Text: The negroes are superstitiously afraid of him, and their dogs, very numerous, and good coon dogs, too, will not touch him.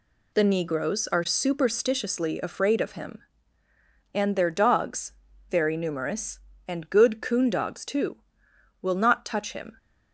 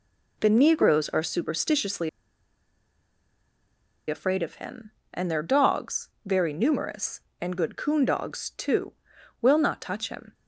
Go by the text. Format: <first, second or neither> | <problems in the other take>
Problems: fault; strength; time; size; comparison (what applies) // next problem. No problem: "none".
first | pauses between "superstitiously" and "afraid"; strong; at 2.0 s; 2.0 s long